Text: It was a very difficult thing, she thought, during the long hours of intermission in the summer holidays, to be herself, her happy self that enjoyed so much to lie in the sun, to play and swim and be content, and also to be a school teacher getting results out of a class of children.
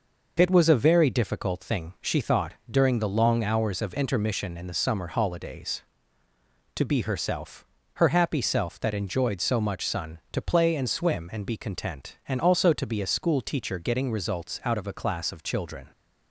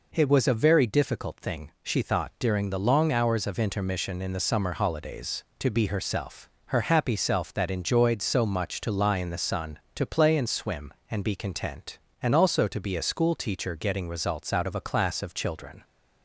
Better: second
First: skips "to lie in the"; at 9.8 s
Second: none

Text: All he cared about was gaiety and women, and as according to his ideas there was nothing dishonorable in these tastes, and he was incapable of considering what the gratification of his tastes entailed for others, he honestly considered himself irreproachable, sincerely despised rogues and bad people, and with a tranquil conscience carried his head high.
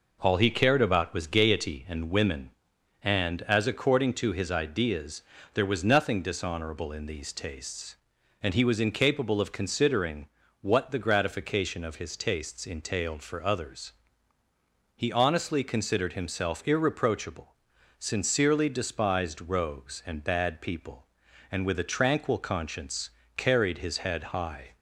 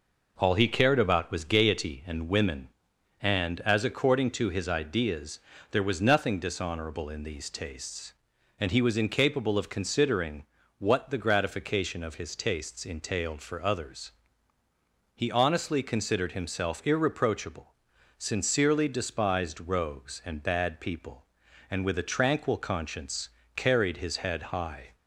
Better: neither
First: pauses between "ideas" and "there"; slight; at 5.2 s; 0.32 s long // pauses between "considering" and "what"; slight; at 10.2 s; 0.34 s long // pauses between "conscience" and "carried"; slight; at 23.0 s; 0.26 s long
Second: pauses between "ideas" and "there"; slight; at 5.3 s; 0.32 s long // pauses between "considering" and "what"; slight; at 10.4 s; 0.34 s long // pauses between "conscience" and "carried"; slight; at 23.2 s; 0.26 s long

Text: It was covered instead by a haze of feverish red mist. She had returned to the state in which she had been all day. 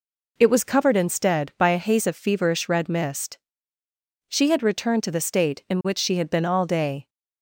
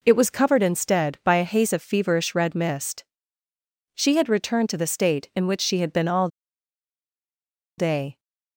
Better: first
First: none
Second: pauses between "all" and "day"; strong; at 6.2 s; 1.5 s long

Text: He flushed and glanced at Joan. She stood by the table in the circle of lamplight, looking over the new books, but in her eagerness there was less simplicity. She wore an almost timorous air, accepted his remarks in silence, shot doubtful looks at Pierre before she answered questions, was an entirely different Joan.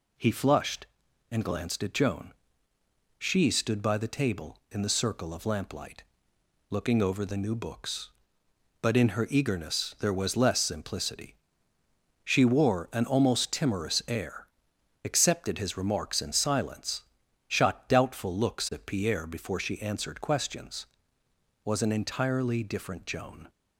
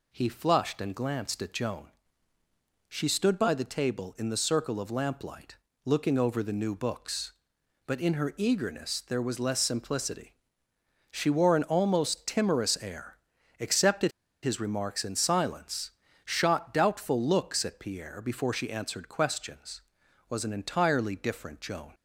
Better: first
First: none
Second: pauses between "accepted" and "his"; slight; at 14.1 s; 0.32 s long

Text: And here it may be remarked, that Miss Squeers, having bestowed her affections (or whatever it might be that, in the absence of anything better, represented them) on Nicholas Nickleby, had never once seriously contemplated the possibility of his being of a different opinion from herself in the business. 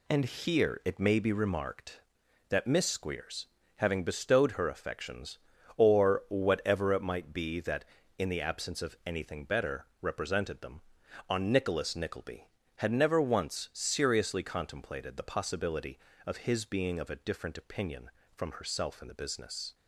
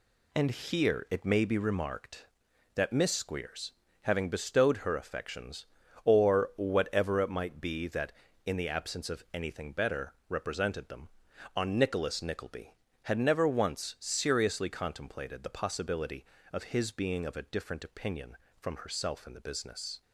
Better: neither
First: none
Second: none

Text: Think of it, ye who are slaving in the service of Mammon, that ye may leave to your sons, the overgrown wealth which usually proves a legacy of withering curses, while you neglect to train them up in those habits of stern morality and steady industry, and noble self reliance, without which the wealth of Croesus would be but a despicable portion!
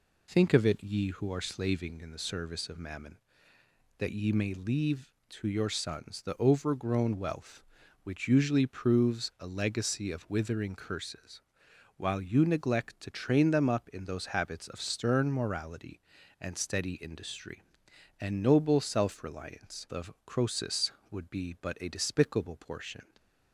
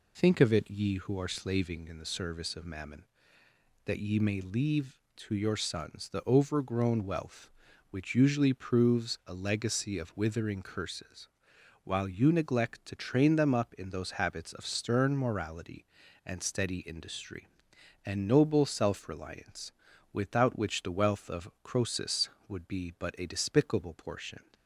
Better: second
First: skips "without which the wealth"; at 19.8 s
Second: none

